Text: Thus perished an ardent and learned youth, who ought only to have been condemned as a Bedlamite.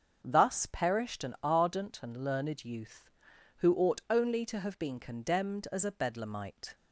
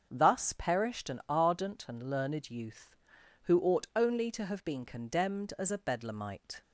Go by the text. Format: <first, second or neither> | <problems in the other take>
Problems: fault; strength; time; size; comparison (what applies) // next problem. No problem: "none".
neither | starts louder than the rest; strong; the same in both